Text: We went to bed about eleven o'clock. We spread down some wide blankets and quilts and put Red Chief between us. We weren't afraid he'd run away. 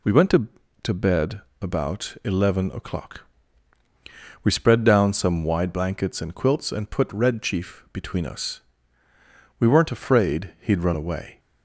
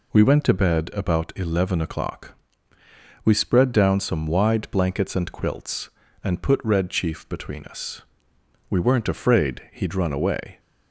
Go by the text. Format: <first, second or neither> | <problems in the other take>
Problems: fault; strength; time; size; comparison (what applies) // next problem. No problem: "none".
second | says "to" twice; at 0.8 s // pauses between "bed" and "about"; slight; at 1.4 s; 0.20 s long